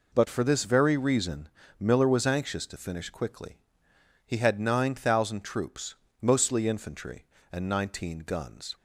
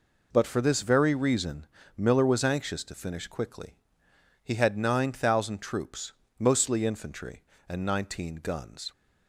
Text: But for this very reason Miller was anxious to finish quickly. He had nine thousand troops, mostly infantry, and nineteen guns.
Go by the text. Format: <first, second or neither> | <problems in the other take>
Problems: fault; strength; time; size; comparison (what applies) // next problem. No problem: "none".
neither | pauses between "reason" and "Miller"; slight; the same in both